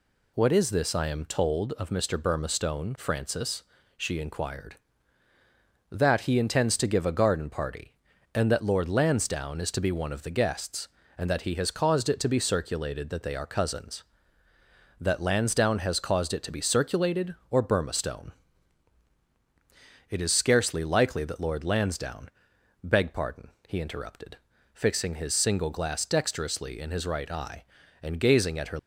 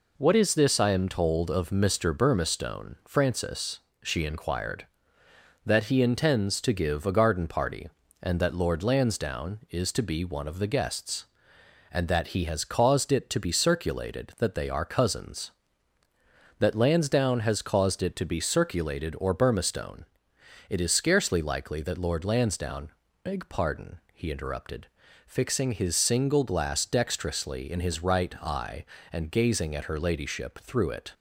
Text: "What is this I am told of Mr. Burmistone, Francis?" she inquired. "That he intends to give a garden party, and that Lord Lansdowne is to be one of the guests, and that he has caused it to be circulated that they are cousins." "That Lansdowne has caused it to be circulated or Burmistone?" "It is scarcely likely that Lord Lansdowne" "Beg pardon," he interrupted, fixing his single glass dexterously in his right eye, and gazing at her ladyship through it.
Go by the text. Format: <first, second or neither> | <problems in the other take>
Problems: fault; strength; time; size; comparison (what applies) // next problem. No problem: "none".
second | pauses between "Lansdowne" and "Beg"; noticeable; at 22.2 s; 0.56 s long; slight in the second // stops before "ladyship through it"; at 28.7 s